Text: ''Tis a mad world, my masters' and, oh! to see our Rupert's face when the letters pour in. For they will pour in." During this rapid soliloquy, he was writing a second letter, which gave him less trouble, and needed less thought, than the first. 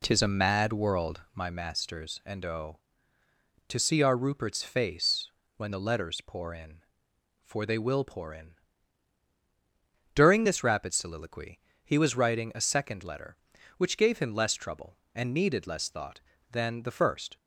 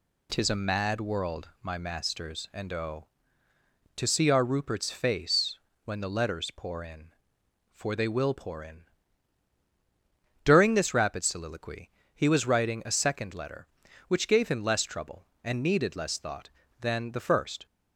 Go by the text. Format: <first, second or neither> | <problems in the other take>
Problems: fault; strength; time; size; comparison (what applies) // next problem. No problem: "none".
second | starts louder than the rest; slight; until 1.5 s; 3 dB // pauses between "face" and "when"; slight; at 5.3 s; 0.24 s long; slight in the second